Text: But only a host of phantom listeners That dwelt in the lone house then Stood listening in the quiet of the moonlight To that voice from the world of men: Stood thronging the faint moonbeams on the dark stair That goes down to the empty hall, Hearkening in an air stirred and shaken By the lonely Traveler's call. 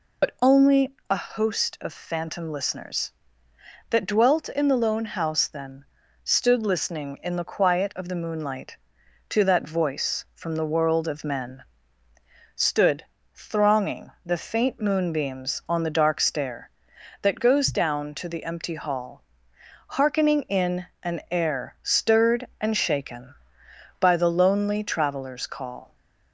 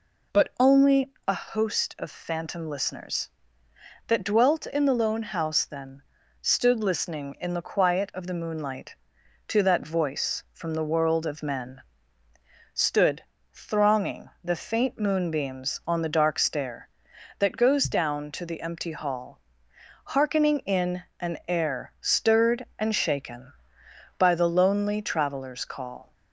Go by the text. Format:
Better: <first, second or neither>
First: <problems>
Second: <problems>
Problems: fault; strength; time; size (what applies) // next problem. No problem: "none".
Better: second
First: loses the start of "But"; at 0.2 s; 75 ms // pauses between "then" and "Stood"; at 5.8 s; 0.38 s long // pauses between "Stood" and "thronging"; slight; at 13.0 s; 0.28 s long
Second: pauses between "then" and "Stood"; at 6.0 s; 0.38 s long // pauses between "Stood" and "thronging"; slight; at 13.2 s; 0.28 s long